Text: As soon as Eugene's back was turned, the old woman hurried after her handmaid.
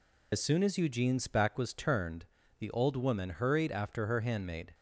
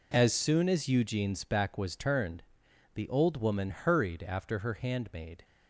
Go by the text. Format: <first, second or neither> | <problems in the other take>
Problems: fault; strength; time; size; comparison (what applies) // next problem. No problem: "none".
second | loses the start of "As"; at 0.3 s; 35 ms